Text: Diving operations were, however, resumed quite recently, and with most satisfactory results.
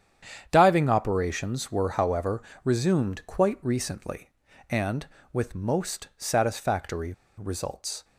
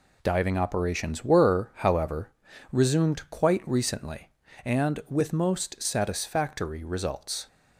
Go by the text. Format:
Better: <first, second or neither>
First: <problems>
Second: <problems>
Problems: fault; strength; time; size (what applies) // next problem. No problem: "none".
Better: second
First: starts louder than the rest; strong; until 1.5 s; 9 dB // pauses between "satisfactory" and "results"; slight; at 7.1 s; 0.23 s long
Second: none